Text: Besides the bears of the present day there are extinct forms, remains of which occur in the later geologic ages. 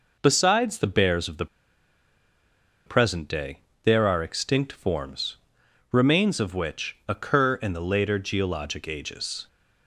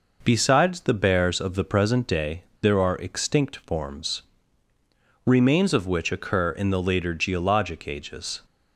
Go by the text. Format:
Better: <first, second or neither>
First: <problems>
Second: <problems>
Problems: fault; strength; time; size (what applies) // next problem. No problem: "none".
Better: second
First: pauses between "the" and "present"; strong; at 1.4 s; 1.4 s long // pauses between "day" and "there"; slight; at 3.5 s; 0.24 s long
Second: pauses between "day" and "there"; slight; at 2.4 s; 0.17 s long